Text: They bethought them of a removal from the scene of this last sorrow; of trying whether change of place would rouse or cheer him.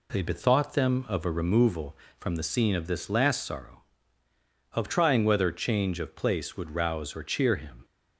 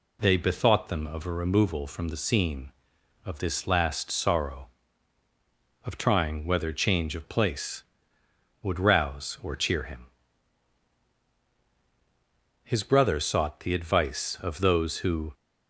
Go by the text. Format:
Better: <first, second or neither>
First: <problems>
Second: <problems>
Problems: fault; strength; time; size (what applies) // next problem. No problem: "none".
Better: first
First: none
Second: goes on to say "His brother sought the advice of those who"; strong; from 12.6 s on; 2.7 s long